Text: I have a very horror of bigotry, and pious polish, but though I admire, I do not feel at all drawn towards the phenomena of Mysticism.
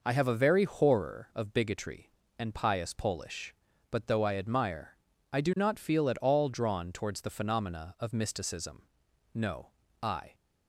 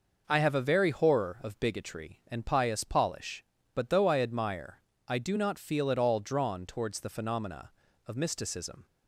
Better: second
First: goes on to say "No I"; noticeable; from 9.3 s on; 1.0 s long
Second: none

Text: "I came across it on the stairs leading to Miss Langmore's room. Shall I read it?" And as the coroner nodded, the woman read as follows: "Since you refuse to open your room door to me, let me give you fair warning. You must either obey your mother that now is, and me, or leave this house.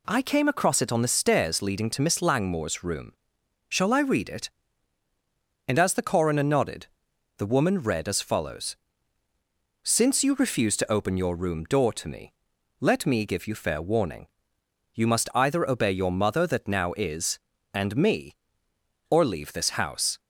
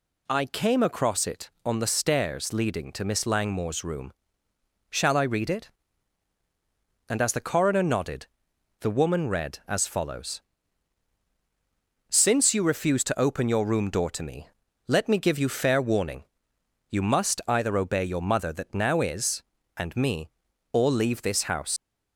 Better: first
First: none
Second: leaves "house" unfinished; at 21.7 s; 90 ms

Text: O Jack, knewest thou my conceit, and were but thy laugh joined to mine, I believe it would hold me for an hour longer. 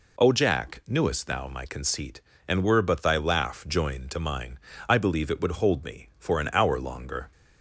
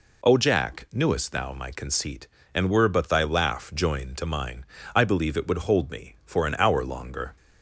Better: neither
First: none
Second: none

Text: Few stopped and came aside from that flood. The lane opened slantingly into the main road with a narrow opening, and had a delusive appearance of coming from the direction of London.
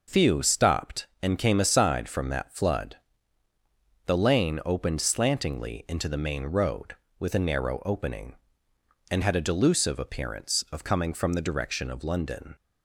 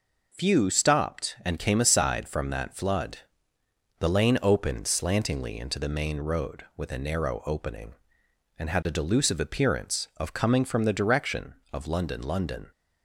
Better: first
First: none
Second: says "London" twice; at 12.2 s

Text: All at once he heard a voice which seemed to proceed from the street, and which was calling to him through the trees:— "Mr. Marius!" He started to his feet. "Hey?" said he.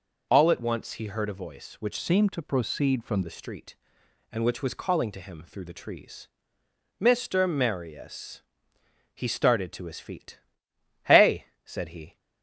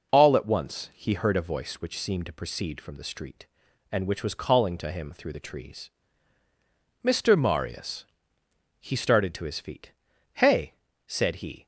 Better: second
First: changes voice from "seemed" to "from"; from 1.9 to 3.2 s; 1.3 s long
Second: none

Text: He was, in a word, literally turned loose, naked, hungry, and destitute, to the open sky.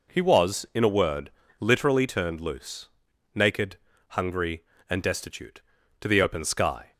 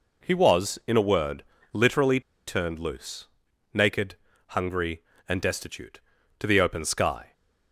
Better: first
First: none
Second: pauses between "literally" and "turned"; slight; at 2.1 s; 0.27 s long

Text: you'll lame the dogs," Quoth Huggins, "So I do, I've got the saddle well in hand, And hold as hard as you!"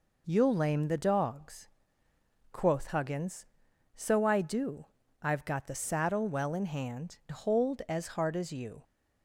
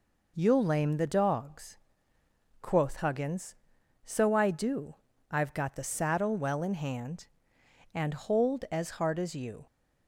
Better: second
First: skips "And"; at 7.2 s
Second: none

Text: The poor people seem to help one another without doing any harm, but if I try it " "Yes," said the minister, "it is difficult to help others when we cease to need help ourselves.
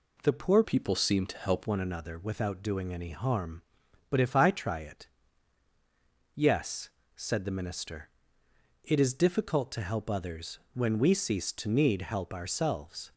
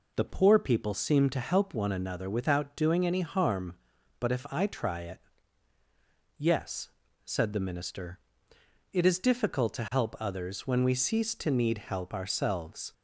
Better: second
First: changes voice from "people" to "help"; from 0.6 to 1.6 s; 1.0 s long // pauses between "others" and "when"; slight; at 10.5 s; 0.16 s long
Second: none

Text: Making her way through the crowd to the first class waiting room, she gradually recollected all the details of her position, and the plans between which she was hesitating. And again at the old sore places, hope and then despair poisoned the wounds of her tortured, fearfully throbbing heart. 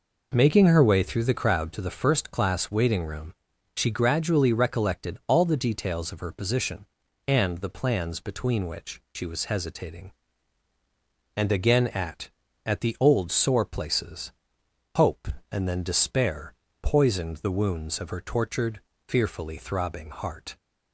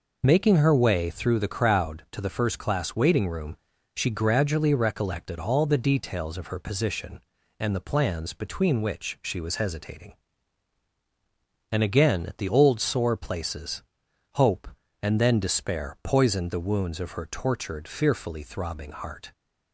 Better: second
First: says "at" twice; at 12.6 s // pauses between "despair" and "poisoned"; slight; at 16.5 s; 0.26 s long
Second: none

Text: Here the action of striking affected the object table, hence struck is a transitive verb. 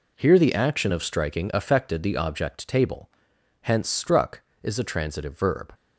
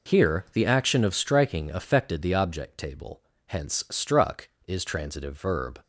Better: first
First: none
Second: skips "a"; at 4.8 s

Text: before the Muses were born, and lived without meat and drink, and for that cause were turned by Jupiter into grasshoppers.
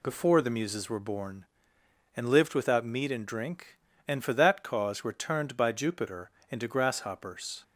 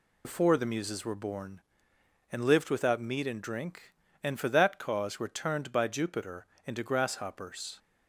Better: first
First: pauses between "Jupiter" and "into"; slight; at 6.2 s; 0.22 s long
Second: loses the start of "before"; at 0.2 s; 65 ms // pauses between "Jupiter" and "into"; slight; at 6.4 s; 0.22 s long

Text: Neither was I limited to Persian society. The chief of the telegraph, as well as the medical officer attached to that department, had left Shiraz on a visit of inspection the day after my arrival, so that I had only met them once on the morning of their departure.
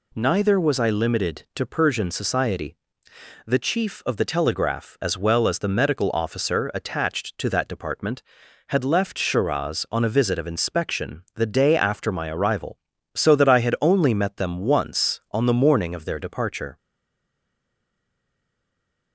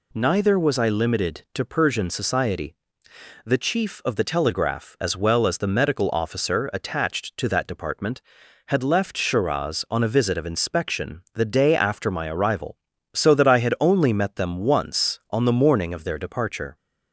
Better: second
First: stays silent after the last word; from 16.7 s on; 2.4 s long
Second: none

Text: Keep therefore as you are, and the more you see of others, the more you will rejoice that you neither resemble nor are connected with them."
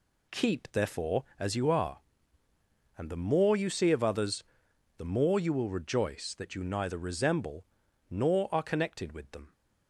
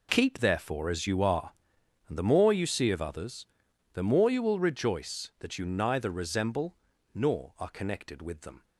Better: neither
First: pauses between "resemble" and "nor"; noticeable; at 7.6 s; 0.46 s long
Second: pauses between "resemble" and "nor"; at 6.7 s; 0.38 s long

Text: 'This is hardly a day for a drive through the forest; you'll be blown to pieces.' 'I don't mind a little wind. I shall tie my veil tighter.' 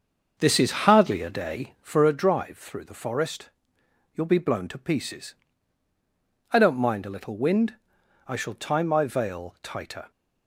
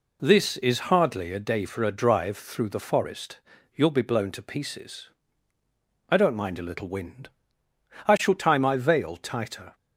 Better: second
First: starts louder than the rest; until 2.1 s; 6 dB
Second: none

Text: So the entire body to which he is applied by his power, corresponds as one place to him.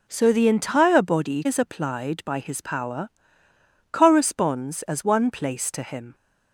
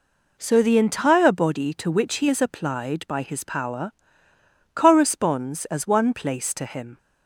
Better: second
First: skips "to which he"; at 1.4 s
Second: none

